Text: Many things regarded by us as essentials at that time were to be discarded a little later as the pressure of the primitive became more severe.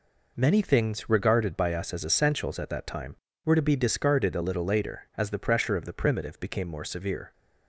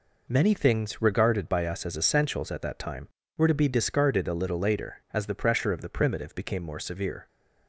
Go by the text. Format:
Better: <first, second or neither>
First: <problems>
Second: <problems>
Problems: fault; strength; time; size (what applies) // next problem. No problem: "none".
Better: neither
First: none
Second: none